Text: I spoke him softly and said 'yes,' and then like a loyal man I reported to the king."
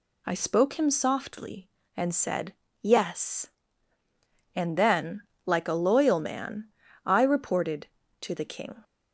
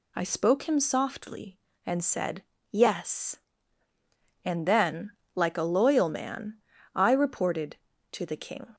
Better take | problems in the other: neither | pauses between "said" and "yes"; slight; the same in both // pauses between "then" and "like"; slight; the same in both // pauses between "man" and "I"; slight; the same in both

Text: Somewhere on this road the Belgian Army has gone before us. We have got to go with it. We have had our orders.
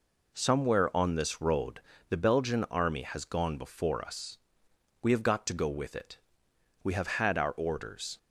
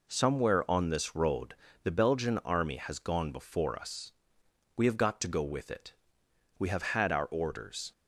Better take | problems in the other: neither | pauses between "road" and "the"; slight; the same in both

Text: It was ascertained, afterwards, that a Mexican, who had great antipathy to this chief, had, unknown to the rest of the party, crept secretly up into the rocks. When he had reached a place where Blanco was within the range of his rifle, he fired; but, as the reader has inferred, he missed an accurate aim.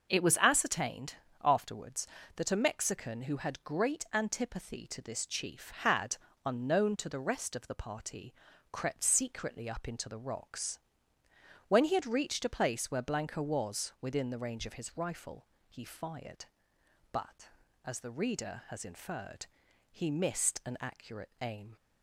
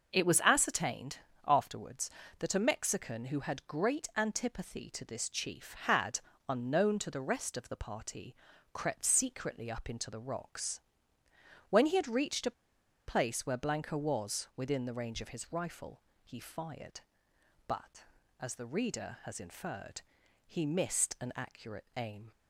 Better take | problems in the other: first | starts louder than the rest; noticeable; until 1.1 s; 6 dB; noticeable in the first // pauses between "a" and "place"; noticeable; at 12.5 s; 0.56 s long

